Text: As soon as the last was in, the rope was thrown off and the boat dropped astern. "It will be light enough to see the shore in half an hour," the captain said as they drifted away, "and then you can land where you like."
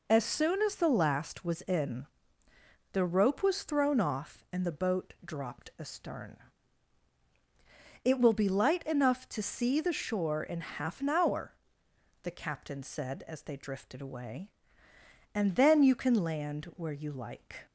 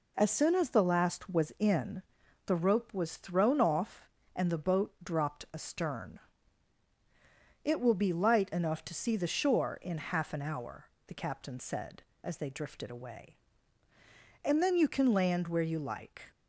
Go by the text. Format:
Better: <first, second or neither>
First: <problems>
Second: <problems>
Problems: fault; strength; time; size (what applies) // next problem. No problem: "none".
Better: neither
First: none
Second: none